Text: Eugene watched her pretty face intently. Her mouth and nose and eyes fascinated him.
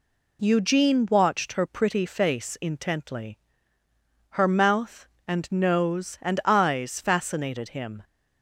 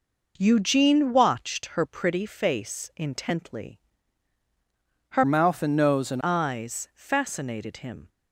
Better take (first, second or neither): first